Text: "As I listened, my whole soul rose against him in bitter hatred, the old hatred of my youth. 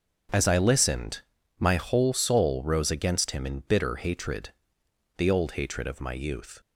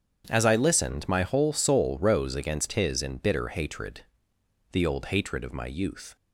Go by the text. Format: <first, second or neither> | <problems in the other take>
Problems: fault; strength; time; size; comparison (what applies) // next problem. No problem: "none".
first | starts louder than the rest; strong; until 1.2 s; 8 dB; also in the first // says "his" for "him"; at 2.7 s